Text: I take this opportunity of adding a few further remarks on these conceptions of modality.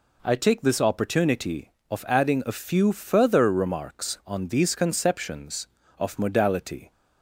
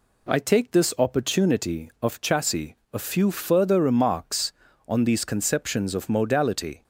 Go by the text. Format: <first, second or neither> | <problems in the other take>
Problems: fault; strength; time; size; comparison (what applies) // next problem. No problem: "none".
first | says "chassis" for "adding"; at 2.1 s